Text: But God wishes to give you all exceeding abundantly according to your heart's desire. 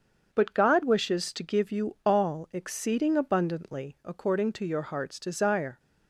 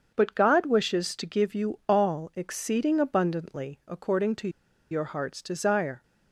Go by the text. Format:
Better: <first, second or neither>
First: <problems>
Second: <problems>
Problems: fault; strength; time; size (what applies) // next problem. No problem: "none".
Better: first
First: starts louder than the rest; until 1.3 s; 7 dB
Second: starts louder than the rest; until 1.1 s; 7 dB // pauses between "to" and "your"; at 4.4 s; 0.42 s long